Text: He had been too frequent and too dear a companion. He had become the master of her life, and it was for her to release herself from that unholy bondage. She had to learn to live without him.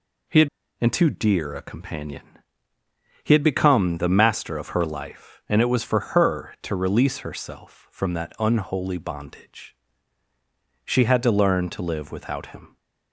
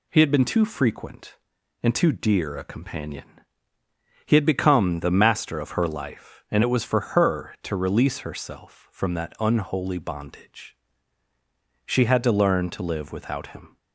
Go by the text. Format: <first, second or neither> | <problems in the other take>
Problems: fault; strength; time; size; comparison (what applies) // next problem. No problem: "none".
second | skips "been too frequent"; at 0.6 s